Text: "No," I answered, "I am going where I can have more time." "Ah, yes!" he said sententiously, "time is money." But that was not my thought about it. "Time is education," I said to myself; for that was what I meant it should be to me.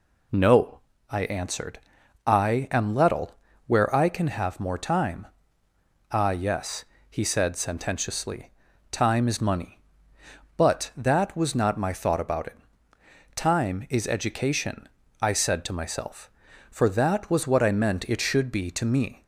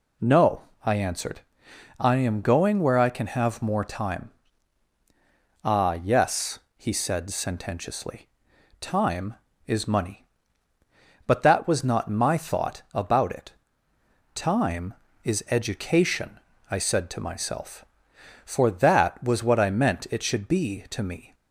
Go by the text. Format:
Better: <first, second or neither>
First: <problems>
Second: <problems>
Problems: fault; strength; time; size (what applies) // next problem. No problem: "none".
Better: second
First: says "lettle" for "going"; at 2.9 s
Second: none